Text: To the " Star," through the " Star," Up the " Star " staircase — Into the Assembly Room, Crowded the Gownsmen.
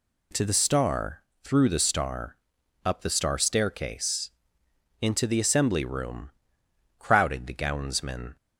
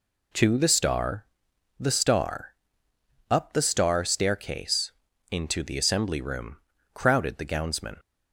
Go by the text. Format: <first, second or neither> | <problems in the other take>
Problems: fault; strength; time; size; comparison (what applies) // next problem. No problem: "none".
first | skips "through"; at 1.5 s